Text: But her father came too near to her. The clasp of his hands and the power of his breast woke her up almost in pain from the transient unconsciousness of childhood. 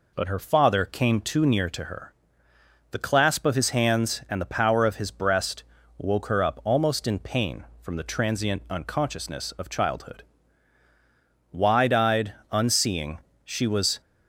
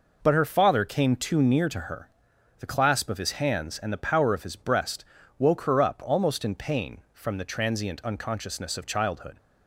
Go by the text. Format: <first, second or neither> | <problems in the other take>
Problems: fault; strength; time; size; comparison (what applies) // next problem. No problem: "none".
second | pauses between "breast" and "woke"; slight; at 5.6 s; 0.34 s long; slight in the second // goes on to say "Wide eyed unseeing she was"; strong; from 11.5 s on; 2.5 s long